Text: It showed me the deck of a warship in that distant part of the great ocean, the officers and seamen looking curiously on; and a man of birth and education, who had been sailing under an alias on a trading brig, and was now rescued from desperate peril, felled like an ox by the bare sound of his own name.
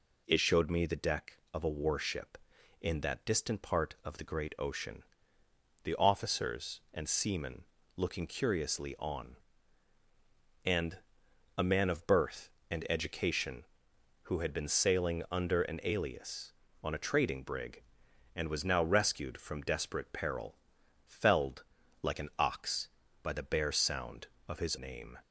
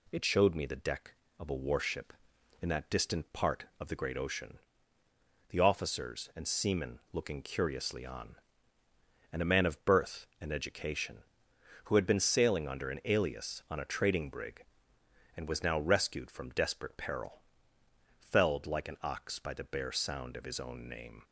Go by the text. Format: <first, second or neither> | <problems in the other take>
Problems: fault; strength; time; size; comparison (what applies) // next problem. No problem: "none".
second | pauses between "seamen" and "looking"; slight; at 7.6 s; 0.34 s long // pauses between "and" and "a"; noticeable; at 10.9 s; 0.58 s long // pauses between "felled" and "like"; at 21.6 s; 0.40 s long // skips "own"; at 24.7 s